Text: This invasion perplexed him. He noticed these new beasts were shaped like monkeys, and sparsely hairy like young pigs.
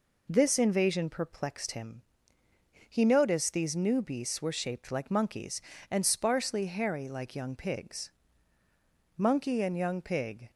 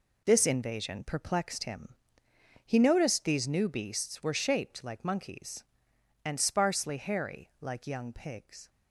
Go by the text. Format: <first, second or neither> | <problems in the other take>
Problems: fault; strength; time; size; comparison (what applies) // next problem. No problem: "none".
second | goes on to say "Monkey and young pig"; from 9.1 s on; 1.3 s long